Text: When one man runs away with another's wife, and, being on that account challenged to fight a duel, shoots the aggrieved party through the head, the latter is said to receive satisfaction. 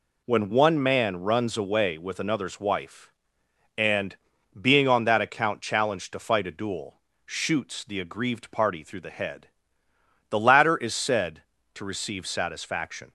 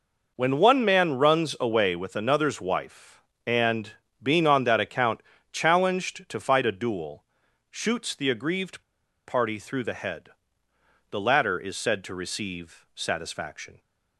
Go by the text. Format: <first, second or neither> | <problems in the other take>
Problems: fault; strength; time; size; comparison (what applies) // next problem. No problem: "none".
first | pauses between "account" and "challenged"; slight; at 5.1 s; 0.32 s long // pauses between "aggrieved" and "party"; at 8.8 s; 0.45 s long